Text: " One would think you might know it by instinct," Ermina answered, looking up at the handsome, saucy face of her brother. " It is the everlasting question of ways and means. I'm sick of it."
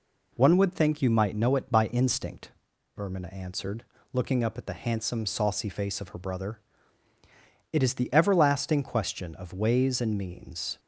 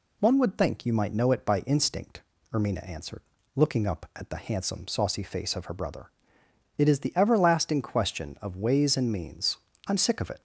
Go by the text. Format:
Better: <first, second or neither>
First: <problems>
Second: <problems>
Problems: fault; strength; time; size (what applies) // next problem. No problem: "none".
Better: second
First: stops before "I'm sick of it"; at 10.7 s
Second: none